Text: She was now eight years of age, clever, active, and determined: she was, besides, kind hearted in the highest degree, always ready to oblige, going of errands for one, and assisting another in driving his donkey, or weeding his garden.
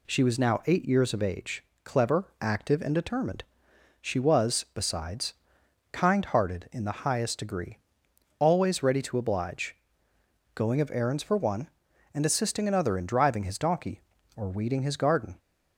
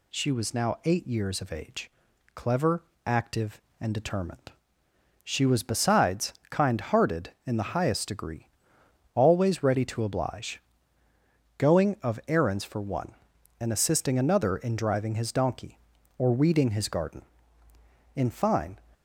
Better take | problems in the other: first | goes on to say "In fine"; noticeable; from 18.1 s on; 0.64 s long

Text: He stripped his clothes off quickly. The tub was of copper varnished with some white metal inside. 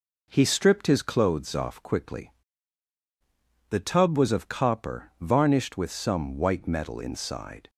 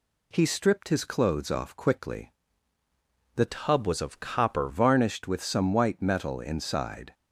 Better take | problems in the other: first | changes voice from "tub" to "copper"; from 3.4 to 4.6 s; 1.2 s long

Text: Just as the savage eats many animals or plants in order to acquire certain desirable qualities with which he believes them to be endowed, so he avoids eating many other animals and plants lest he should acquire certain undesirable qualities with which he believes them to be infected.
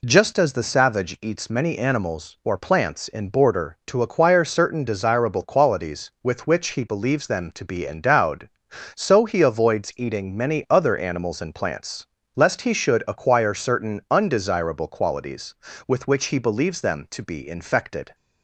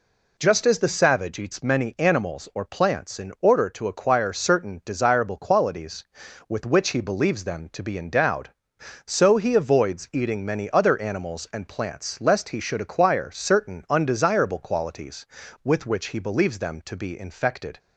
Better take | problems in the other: second | says "border" for "order"; at 3.2 s // pauses between "plants" and "lest"; slight; at 12.0 s; 0.30 s long

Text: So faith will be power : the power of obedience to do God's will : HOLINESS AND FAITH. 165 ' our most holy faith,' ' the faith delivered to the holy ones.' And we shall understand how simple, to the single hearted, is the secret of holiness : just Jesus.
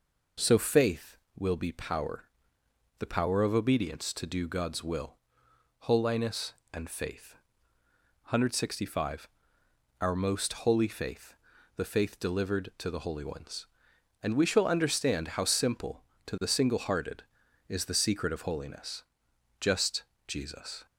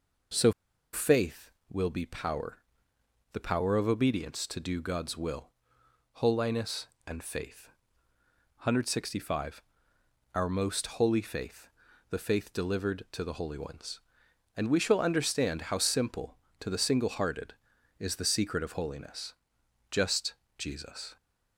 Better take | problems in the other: first | pauses between "So" and "faith"; at 0.5 s; 0.42 s long // pauses between "just" and "Jesus"; slight; at 20.3 s; 0.24 s long; slight in the first

